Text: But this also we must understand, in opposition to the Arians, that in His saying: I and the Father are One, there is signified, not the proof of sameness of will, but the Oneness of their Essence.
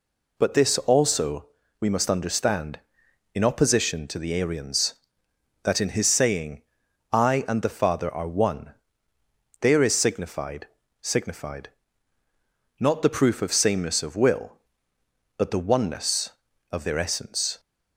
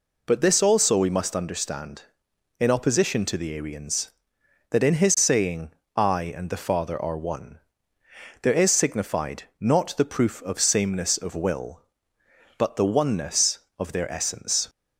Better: second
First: pauses between "also" and "we"; slight; at 1.4 s; 0.32 s long // says "signified" twice; at 11.0 s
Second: none

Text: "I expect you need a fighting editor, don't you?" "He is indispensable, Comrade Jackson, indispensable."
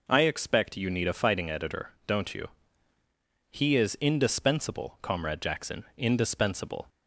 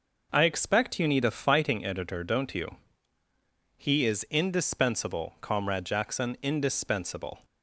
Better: neither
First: none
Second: none

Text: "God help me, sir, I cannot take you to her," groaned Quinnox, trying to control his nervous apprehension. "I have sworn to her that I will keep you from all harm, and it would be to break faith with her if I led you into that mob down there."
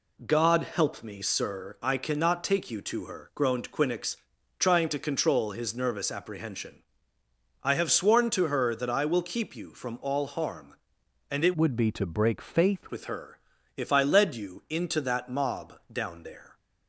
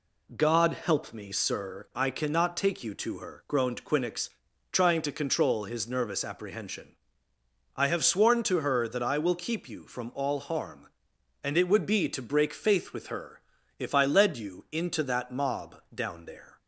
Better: second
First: changes voice from "would" to "faith"; from 11.5 to 12.8 s; 1.3 s long // pauses between "her" and "if"; slight; at 13.3 s; 0.36 s long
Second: pauses between "her" and "if"; slight; at 13.4 s; 0.36 s long

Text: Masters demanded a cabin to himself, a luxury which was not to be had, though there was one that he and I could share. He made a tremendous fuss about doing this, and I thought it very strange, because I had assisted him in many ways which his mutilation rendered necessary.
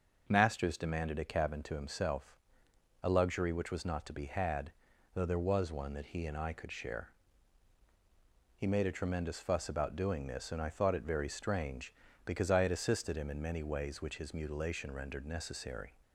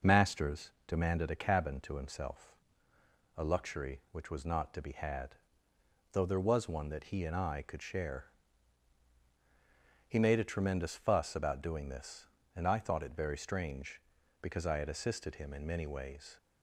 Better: first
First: none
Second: stops before "which his mutilation rendered necessary"; at 16.3 s

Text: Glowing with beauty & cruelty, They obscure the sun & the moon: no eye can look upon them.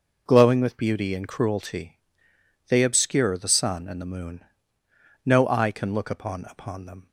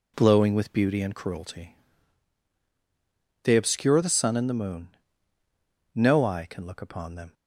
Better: second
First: says "upon" twice; at 6.4 s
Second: none

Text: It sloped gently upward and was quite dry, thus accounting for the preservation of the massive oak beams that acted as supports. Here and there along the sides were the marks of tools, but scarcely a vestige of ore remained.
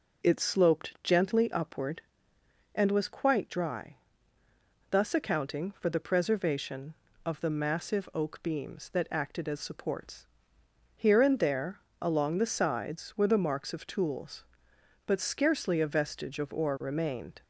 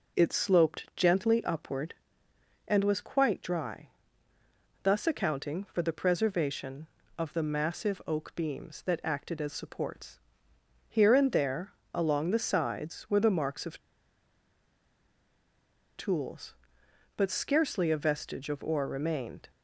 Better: first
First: pauses between "there" and "along"; slight; at 11.7 s; 0.20 s long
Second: pauses between "there" and "along"; slight; at 11.7 s; 0.20 s long // pauses between "of" and "tools"; strong; at 13.7 s; 2.1 s long

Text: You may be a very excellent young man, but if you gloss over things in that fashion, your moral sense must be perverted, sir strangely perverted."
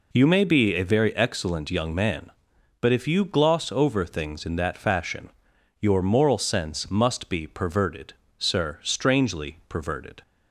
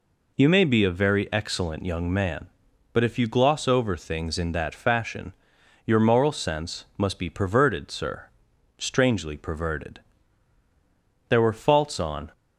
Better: first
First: none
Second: pauses between "sir" and "strangely"; noticeable; at 8.2 s; 0.50 s long // goes on to say "There were faults on"; noticeable; from 11.2 s on; 1.0 s long

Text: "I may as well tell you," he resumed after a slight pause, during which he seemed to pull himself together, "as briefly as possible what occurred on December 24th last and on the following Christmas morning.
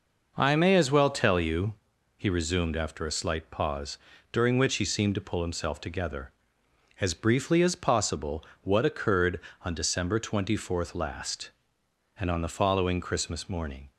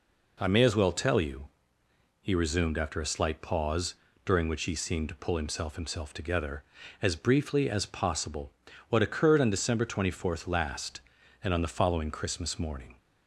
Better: first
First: pauses between "possible" and "what"; slight; at 8.4 s; 0.20 s long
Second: says "himself" twice; at 5.7 s // pauses between "possible" and "what"; slight; at 8.5 s; 0.36 s long

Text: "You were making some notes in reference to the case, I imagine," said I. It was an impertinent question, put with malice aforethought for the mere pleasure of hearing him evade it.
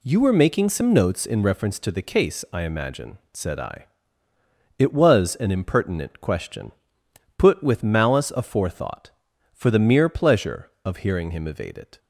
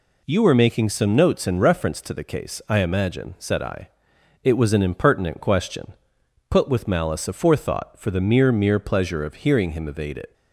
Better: first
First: none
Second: says "mere" twice; at 8.5 s

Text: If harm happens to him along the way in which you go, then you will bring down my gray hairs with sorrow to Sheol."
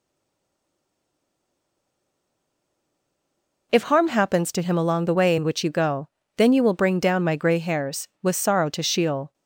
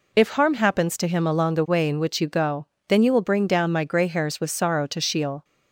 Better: second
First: stays silent before the first word; strong; until 3.7 s; 3.7 s long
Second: none

